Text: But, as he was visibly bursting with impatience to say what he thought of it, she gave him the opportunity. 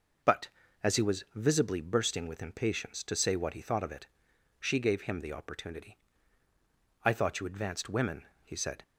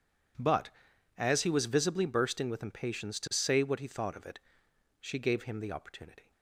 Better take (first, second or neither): second